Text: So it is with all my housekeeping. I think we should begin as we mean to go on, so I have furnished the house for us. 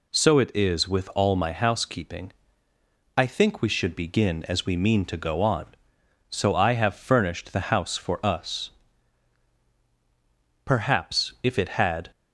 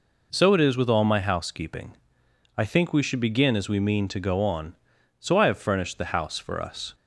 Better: second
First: goes on to say "Perhaps if it had"; from 10.6 s on; 1.4 s long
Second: none

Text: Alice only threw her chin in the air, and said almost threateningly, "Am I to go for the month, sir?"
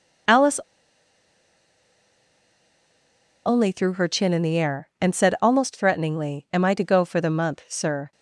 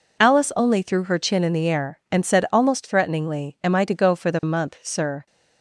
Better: second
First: pauses between "Alice" and "only"; strong; at 0.5 s; 2.8 s long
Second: none

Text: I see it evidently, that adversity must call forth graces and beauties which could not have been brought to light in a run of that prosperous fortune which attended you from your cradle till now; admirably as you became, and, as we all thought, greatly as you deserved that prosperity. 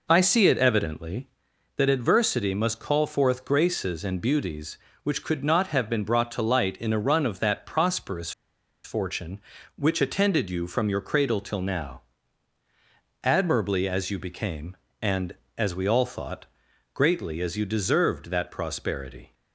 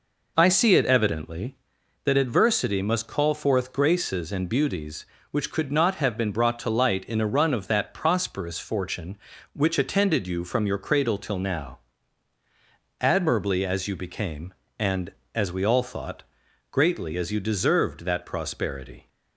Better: second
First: pauses between "prosperous" and "fortune"; noticeable; at 8.3 s; 0.53 s long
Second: none

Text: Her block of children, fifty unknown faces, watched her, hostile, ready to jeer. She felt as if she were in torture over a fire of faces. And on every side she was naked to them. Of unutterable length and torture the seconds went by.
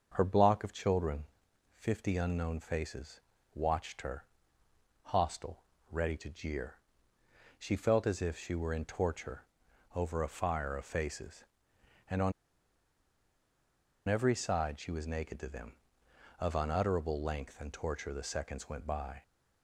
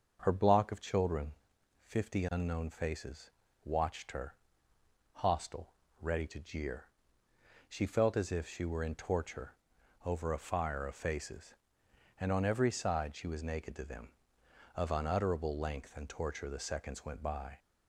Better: second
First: starts louder than the rest; until 1.1 s; 6.5 dB // pauses between "torture" and "over"; noticeable; at 9.4 s; 0.50 s long // pauses between "on" and "every"; strong; at 12.3 s; 1.7 s long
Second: starts louder than the rest; until 1.2 s; 6.5 dB // pauses between "torture" and "over"; noticeable; at 9.5 s; 0.50 s long

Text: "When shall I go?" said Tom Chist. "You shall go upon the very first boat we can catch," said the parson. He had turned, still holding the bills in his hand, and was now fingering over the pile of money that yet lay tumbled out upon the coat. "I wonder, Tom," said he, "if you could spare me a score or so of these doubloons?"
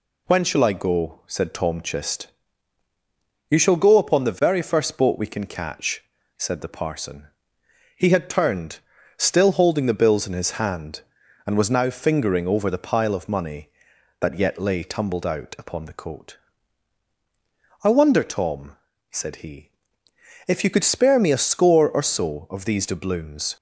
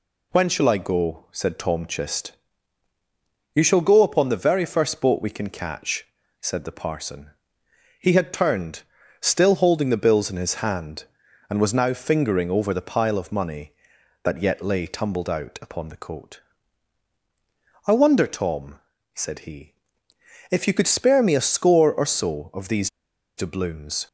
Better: first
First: none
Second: pauses between "these" and "doubloons"; noticeable; at 22.8 s; 0.47 s long

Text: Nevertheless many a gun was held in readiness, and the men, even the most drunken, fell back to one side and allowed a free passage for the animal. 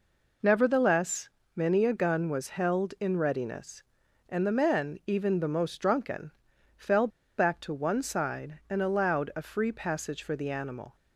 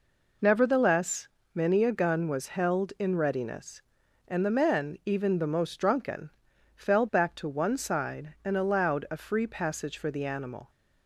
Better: second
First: pauses between "Nevertheless" and "many"; slight; at 1.2 s; 0.26 s long // pauses between "fell" and "back"; slight; at 7.0 s; 0.29 s long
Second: pauses between "Nevertheless" and "many"; slight; at 1.2 s; 0.26 s long

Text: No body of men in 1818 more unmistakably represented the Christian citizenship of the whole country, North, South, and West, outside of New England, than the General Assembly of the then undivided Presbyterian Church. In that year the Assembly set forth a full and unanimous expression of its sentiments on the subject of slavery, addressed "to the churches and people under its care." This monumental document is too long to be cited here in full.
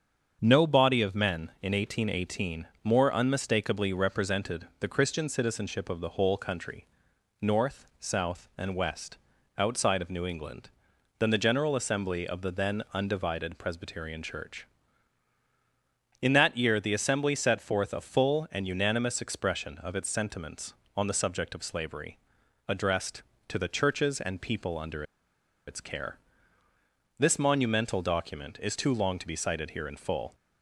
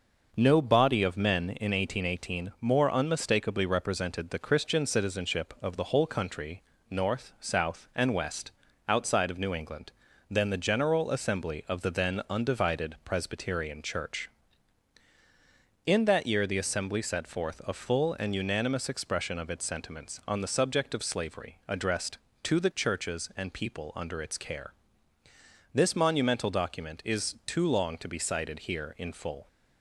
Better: second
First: starts louder than the rest; until 1.4 s; 7 dB // pauses between "under" and "its"; noticeable; at 25.0 s; 0.64 s long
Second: none

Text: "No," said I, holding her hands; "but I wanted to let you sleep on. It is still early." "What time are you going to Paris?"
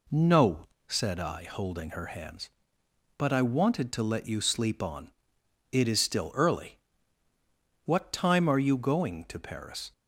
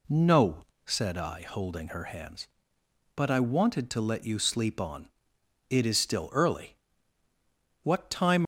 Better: first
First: none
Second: stops before "are you going to Paris"; at 8.4 s

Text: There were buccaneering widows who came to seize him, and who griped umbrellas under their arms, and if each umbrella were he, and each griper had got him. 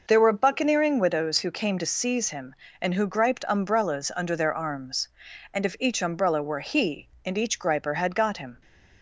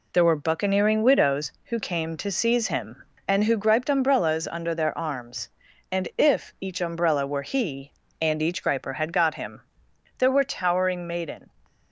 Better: first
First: none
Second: goes on to say "There were towering maiden"; from 10.1 s on; 1.3 s long

